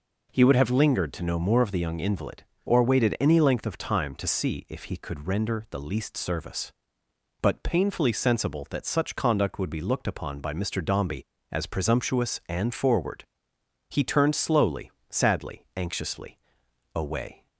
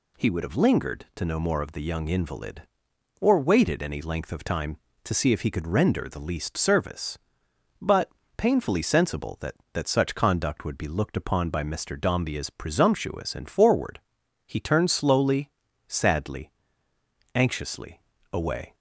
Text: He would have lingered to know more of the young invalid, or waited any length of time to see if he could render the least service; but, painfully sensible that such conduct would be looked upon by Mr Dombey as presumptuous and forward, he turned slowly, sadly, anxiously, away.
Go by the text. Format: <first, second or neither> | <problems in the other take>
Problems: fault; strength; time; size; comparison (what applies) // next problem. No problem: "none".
first | says "that" twice; at 9.7 s